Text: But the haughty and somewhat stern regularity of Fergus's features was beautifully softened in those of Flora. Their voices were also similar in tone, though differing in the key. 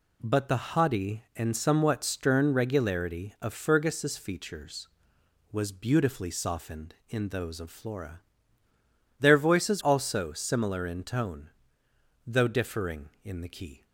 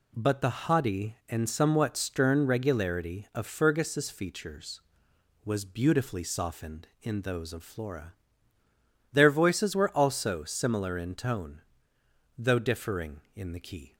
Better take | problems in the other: second | skips "were"; at 9.8 s

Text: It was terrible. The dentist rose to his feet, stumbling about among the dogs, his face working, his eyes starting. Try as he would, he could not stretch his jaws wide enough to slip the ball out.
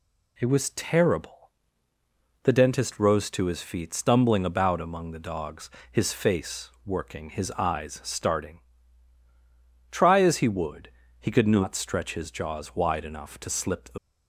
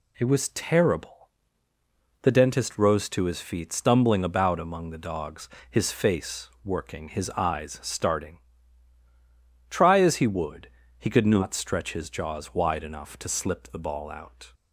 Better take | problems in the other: second | pauses between "face" and "working"; slight; at 6.6 s; 0.16 s long; slight in the second // stops before "ball out"; at 13.9 s

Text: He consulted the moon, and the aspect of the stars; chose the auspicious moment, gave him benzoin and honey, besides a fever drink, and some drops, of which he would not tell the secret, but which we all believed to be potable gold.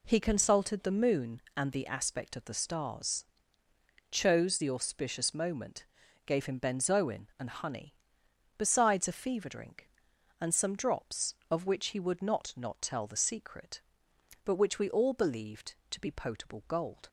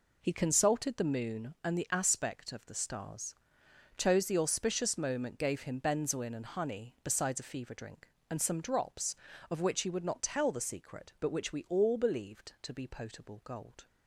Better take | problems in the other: second | says "not" twice; at 12.5 s

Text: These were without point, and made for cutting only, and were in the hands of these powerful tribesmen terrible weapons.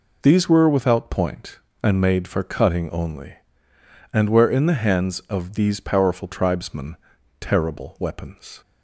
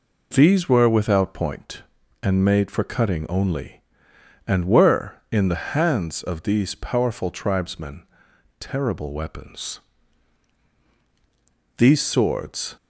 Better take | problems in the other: first | pauses between "tribesmen" and "terrible"; noticeable; at 8.0 s; 0.52 s long; also in the first // goes on to say "These swords"; noticeable; from 11.7 s on; 1.0 s long

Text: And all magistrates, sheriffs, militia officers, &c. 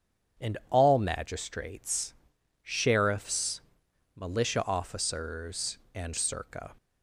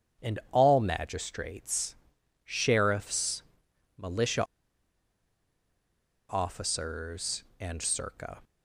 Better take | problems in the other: first | starts louder than the rest; strong; until 1.3 s; 7.5 dB; strong in the first // pauses between "militia" and "officers"; strong; at 4.4 s; 1.8 s long

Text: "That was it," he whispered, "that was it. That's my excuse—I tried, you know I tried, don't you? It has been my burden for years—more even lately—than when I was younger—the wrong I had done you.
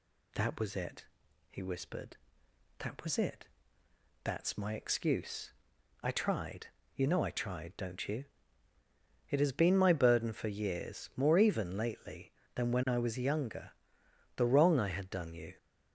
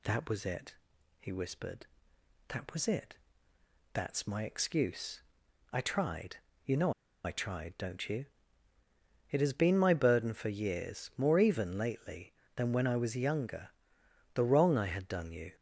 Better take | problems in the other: first | pauses between "know" and "I"; slight; at 6.9 s; 0.32 s long

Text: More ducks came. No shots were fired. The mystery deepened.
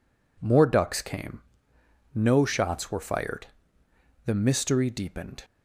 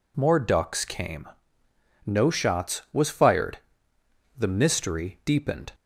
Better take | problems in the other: first | says "was" for "were"; at 2.9 s

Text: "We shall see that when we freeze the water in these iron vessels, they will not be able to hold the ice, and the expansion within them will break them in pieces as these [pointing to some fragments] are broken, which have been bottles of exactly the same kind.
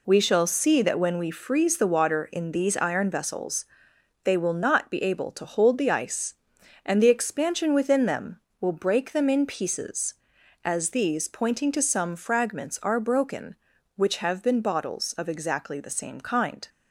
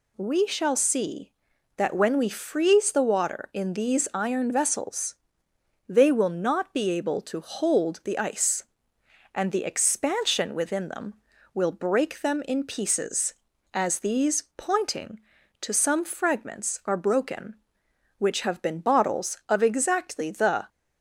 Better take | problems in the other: first | pauses between "these" and "pointing"; slight; at 14.4 s; 0.16 s long // stops before "same kind"; at 20.6 s

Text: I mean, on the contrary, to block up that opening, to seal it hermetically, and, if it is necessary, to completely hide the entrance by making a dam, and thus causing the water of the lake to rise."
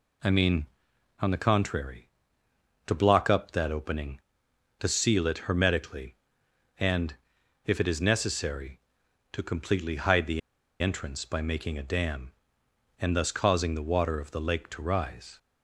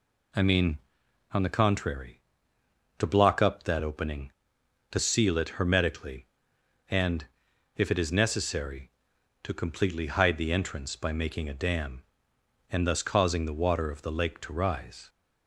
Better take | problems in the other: second | pauses between "the" and "entrance"; at 10.4 s; 0.41 s long

